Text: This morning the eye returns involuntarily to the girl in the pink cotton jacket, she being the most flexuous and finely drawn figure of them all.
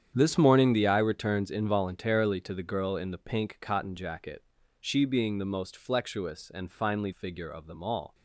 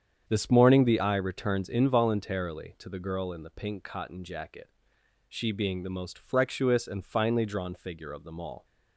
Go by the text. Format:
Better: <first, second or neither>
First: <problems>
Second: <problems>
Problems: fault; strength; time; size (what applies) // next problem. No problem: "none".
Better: second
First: starts louder than the rest; strong; until 1.1 s; 9 dB // skips "drawn"; at 7.1 s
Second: starts louder than the rest; strong; until 1.3 s; 8 dB